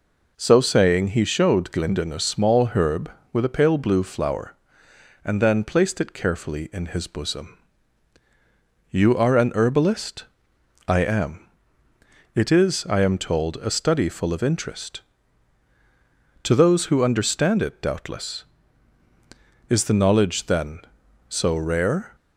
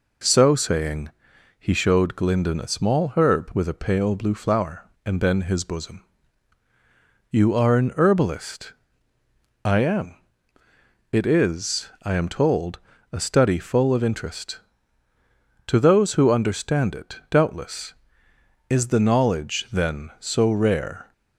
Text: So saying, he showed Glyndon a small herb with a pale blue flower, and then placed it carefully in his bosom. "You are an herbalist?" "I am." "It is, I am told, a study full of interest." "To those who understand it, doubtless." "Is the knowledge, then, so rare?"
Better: first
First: none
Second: skips "placed it carefully in"; at 5.4 s

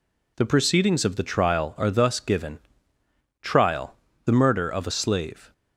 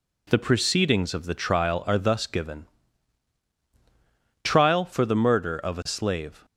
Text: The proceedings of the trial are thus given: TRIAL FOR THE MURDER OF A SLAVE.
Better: second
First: skips "FOR"; at 4.0 s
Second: none

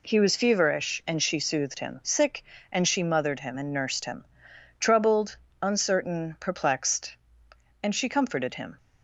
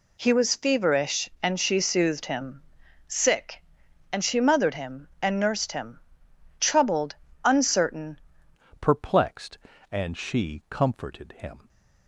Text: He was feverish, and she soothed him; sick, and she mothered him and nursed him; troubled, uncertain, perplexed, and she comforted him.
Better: first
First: none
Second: changes voice at "perplexed"; from 8.7 s on; 2.9 s long

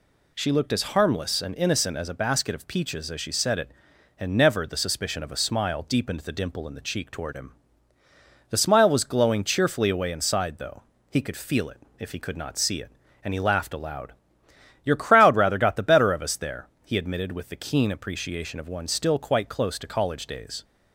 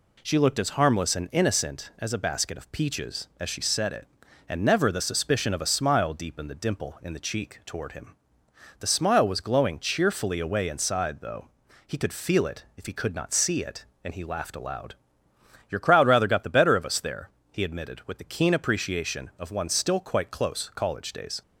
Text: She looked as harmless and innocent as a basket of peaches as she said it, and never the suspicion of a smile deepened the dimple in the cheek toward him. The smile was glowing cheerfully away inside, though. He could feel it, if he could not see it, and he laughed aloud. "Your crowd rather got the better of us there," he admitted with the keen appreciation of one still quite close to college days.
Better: first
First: none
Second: skips "to"; at 20.7 s

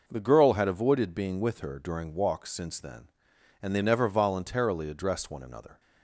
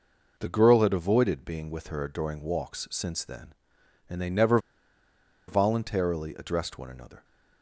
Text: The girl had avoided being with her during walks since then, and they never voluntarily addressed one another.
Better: first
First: none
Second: pauses between "never" and "voluntarily"; noticeable; at 4.5 s; 0.89 s long

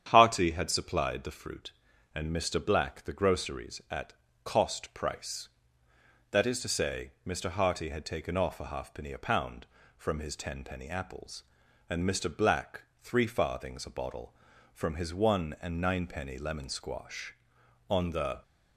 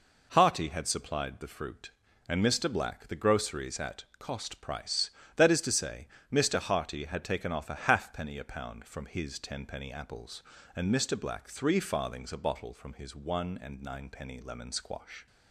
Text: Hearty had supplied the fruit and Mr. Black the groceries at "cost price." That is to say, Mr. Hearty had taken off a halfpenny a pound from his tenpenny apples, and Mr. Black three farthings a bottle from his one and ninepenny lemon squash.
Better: second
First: starts louder than the rest; strong; until 1.1 s; 9 dB // pauses between "at" and "cost"; slight; at 4.1 s; 0.32 s long // pauses between "Black" and "three"; slight; at 12.8 s; 0.16 s long // goes on to say "On the"; from 17.8 s on; 0.52 s long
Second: pauses between "at" and "cost"; slight; at 4.0 s; 0.16 s long

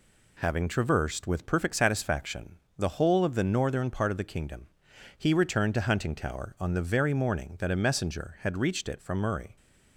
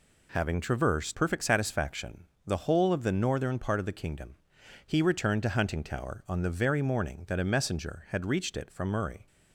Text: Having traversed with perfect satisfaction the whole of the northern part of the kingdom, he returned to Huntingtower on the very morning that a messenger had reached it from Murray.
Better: first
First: pauses between "satisfaction" and "the"; slight; at 2.5 s; 0.20 s long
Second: skips "with"; at 1.1 s // pauses between "satisfaction" and "the"; slight; at 2.2 s; 0.20 s long

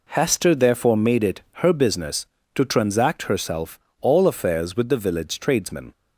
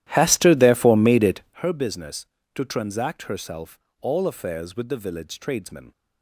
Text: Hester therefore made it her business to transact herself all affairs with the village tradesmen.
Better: first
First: pauses between "it" and "her"; slight; at 1.4 s; 0.20 s long // pauses between "herself" and "all"; slight; at 3.7 s; 0.22 s long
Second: starts louder than the rest; strong; until 1.6 s; 13 dB // pauses between "it" and "her"; slight; at 1.4 s; 0.20 s long // pauses between "herself" and "all"; slight; at 3.7 s; 0.22 s long

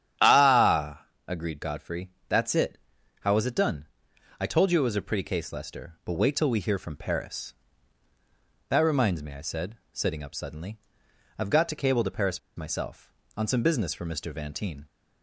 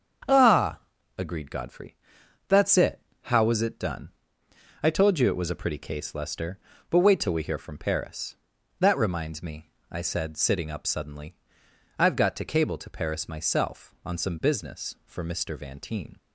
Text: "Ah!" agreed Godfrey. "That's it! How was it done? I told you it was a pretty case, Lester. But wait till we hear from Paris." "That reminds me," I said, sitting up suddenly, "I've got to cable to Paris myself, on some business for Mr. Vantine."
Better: second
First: starts louder than the rest; strong; until 1.4 s; 9.5 dB // pauses between "Paris" and "myself"; slight; at 12.3 s; 0.16 s long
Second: starts louder than the rest; strong; until 1.6 s; 7.5 dB

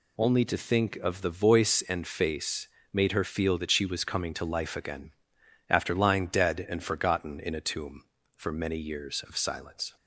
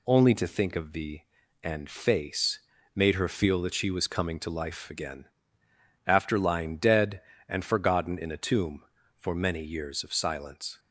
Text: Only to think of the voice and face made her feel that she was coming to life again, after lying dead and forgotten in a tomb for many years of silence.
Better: first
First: pauses between "face" and "made"; slight; at 2.6 s; 0.24 s long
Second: skips "voice"; at 1.4 s // pauses between "face" and "made"; slight; at 2.5 s; 0.36 s long

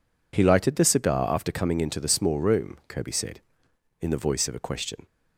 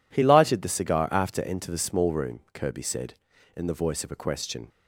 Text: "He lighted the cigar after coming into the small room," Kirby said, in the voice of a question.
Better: first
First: none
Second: skips "coming"; at 1.3 s

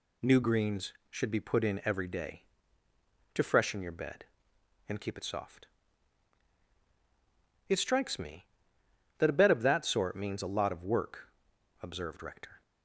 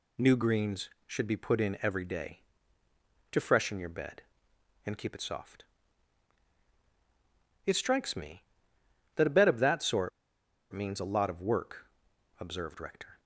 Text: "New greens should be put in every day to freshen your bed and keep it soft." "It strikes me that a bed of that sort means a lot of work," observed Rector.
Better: first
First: none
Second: pauses between "sort" and "means"; noticeable; at 10.1 s; 0.63 s long

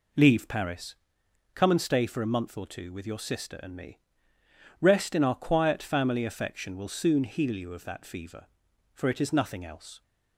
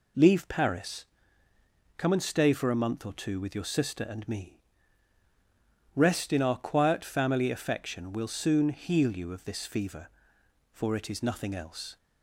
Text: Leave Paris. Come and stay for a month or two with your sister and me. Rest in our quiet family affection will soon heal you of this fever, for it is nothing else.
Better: second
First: says "that" for "this"; at 7.8 s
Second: none

